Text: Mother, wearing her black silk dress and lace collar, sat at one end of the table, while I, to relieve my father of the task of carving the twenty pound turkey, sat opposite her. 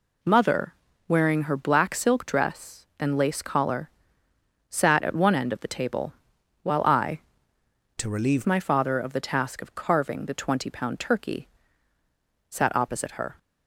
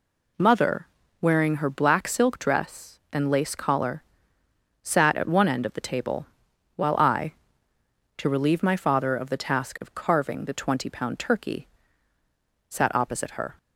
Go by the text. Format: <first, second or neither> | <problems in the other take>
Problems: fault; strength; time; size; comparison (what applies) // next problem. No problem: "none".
second | changes voice from "to" to "relieve"; from 7.9 to 8.4 s; 0.5 s long